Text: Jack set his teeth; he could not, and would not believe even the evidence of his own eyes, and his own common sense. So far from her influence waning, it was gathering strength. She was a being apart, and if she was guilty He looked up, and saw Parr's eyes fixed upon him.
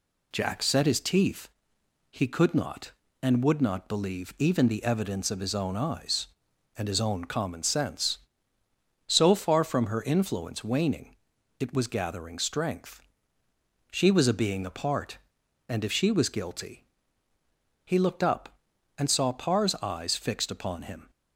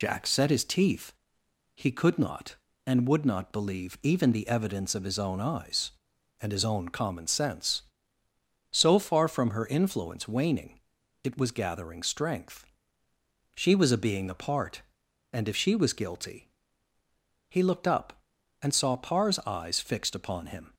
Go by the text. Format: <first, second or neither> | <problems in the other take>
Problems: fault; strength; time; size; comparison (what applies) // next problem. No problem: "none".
first | loses the start of "Jack"; at 0.0 s; 45 ms // pauses between "guilty" and "He"; noticeable; at 16.4 s; 0.98 s long; noticeable in the first